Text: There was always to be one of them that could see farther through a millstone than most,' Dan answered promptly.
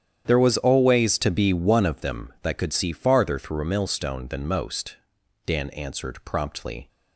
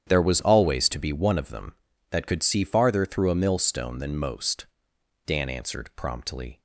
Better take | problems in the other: neither | starts louder than the rest; strong; the same in both

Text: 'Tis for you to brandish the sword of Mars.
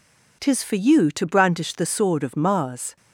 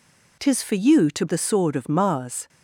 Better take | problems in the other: first | skips "brandish"; at 1.2 s

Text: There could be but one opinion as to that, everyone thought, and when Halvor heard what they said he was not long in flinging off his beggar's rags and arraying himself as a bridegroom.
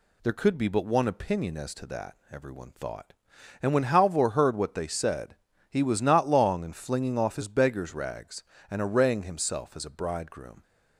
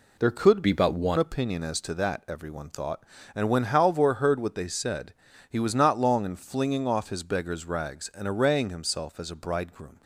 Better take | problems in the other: first | changes voice from "be" to "one"; from 0.6 to 1.1 s; 0.5 s long // pauses between "said" and "he"; slight; at 5.1 s; 0.36 s long; slight in the first

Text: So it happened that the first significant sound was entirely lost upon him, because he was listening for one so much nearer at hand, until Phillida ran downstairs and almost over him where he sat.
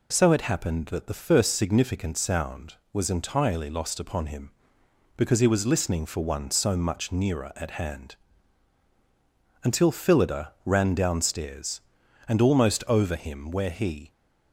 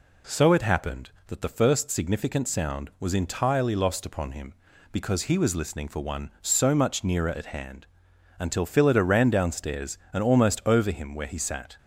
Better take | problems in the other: second | stops before "sat"; at 14.1 s

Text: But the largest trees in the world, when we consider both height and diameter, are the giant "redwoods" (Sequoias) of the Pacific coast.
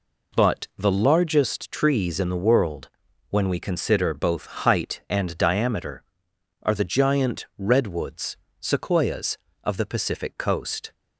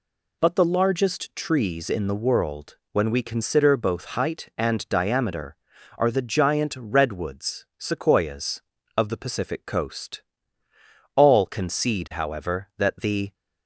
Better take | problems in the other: first | goes on to say "All concede however that the"; strong; from 11.1 s on; 2.1 s long

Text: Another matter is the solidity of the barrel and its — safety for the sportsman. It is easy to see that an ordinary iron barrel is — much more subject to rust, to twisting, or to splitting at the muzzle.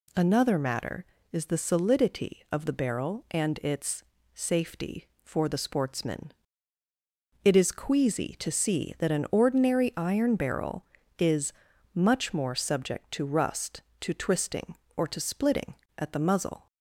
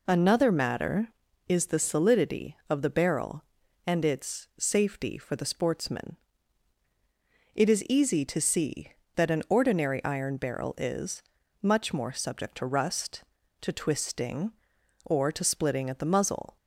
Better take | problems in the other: second | says "queasy" for "easy"; at 7.7 s

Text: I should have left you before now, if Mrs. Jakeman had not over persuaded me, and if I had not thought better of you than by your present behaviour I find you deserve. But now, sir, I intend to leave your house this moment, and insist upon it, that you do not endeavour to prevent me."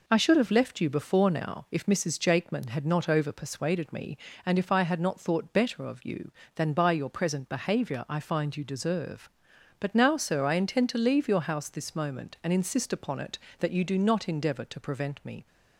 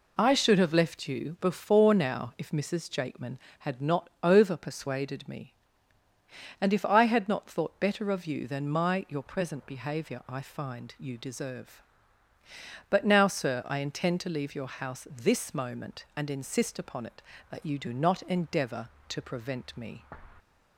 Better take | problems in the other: first | says "my" for "by"; at 8.6 s

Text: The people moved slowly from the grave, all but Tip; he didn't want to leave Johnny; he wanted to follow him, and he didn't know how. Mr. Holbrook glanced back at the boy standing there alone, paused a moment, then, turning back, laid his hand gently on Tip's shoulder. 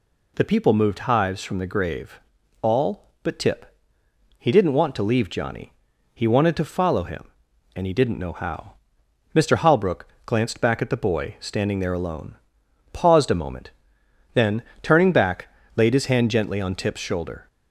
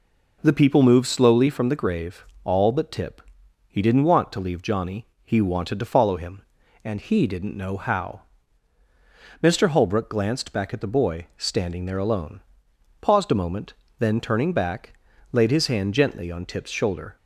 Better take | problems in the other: second | says "hives" for "slowly"; at 0.9 s // pauses between "Holbrook" and "glanced"; slight; at 10.0 s; 0.16 s long

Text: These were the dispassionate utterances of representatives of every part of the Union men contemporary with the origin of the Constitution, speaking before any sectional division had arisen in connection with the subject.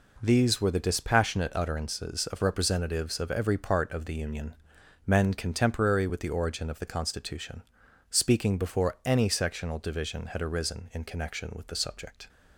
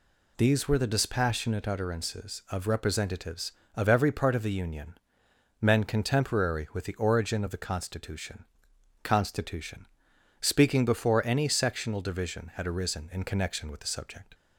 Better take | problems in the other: first | pauses between "Union" and "men"; noticeable; at 4.9 s; 0.64 s long; noticeable in the first // says "Constitution" twice; at 9.0 s

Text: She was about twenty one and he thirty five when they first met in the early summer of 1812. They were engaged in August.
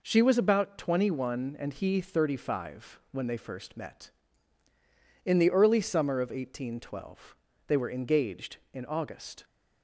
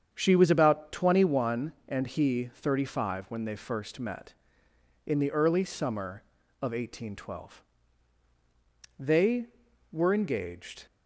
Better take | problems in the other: first | starts louder than the rest; strong; until 1.1 s; 7.5 dB // stops before "in August"; at 10.8 s

